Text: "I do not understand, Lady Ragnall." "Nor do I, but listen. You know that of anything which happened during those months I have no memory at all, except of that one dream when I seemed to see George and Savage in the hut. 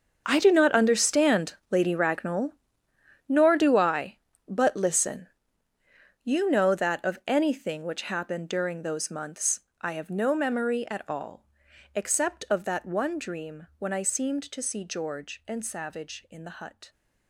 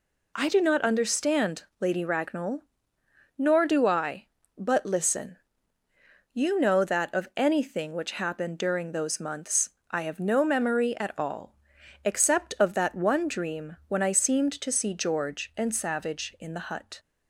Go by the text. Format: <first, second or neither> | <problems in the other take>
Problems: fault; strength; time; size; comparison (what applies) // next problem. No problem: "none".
second | gets quieter; strong; throughout; 16 dB // pauses between "months" and "I"; slight; at 9.5 s; 0.20 s long; slight in the second